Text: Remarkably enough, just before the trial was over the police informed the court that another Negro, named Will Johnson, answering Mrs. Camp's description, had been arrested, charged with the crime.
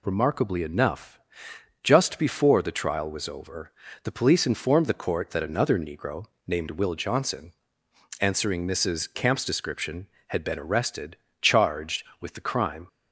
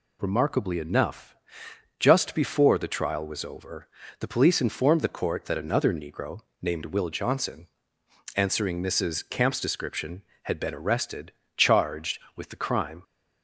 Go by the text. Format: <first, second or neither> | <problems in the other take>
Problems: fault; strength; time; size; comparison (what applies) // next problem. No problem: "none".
neither | pauses between "over" and "the"; slight; the same in both